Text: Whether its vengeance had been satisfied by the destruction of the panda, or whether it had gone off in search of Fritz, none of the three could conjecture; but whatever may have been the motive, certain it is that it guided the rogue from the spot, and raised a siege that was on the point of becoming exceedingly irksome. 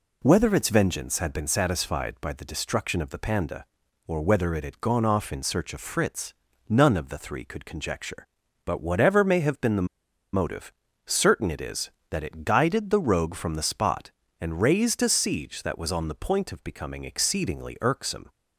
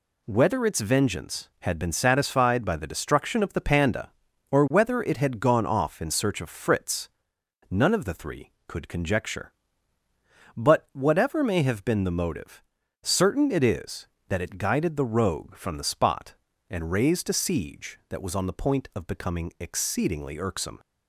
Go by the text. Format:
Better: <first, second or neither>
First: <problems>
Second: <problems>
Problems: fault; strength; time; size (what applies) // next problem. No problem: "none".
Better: second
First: pauses between "the" and "motive"; noticeable; at 9.8 s; 0.48 s long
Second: none